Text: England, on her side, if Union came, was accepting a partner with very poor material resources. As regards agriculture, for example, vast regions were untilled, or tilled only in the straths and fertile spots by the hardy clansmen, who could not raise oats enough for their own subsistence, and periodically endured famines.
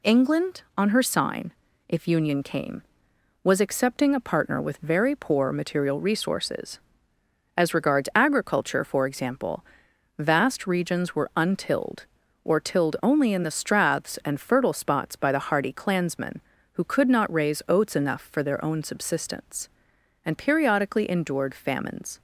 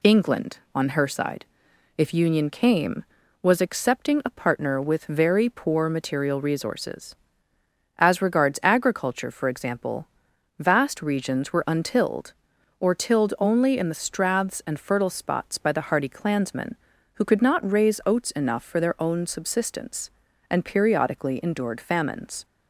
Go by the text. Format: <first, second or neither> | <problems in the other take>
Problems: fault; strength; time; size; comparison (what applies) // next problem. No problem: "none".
second | says "sign" for "side"; at 1.0 s